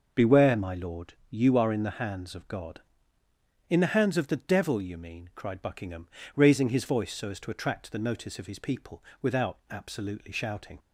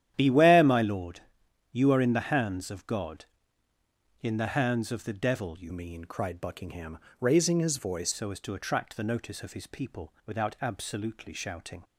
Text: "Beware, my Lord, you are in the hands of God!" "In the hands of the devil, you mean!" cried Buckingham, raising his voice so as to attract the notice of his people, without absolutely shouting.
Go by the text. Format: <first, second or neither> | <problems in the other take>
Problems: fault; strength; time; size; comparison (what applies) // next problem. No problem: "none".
first | starts louder than the rest; strong; until 1.1 s; 11 dB // changes voice from "mean" to "voice"; from 5.7 to 8.1 s; 2.4 s long